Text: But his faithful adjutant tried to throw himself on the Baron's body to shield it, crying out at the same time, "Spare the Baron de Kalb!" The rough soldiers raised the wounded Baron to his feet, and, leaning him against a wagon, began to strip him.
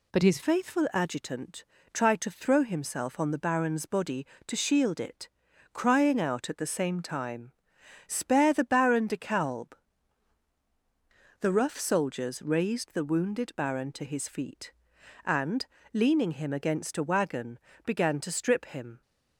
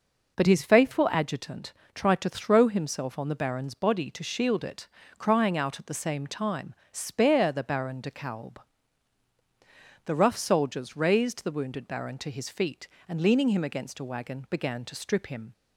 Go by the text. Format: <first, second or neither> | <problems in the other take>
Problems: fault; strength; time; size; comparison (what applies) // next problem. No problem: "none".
second | changes voice at "faithful"; from 0.4 s on; 18.6 s long // pauses between "adjutant" and "tried"; slight; at 1.6 s; 0.30 s long; slight in the second